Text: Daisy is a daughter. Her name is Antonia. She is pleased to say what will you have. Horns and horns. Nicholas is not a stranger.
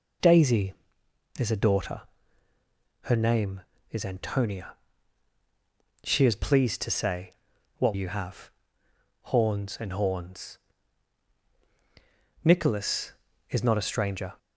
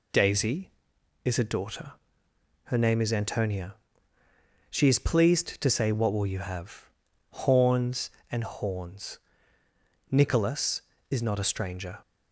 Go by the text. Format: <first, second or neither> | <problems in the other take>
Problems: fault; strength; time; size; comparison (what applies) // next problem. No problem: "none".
second | pauses between "say" and "what"; noticeable; at 7.3 s; 0.48 s long // skips "will"; at 7.9 s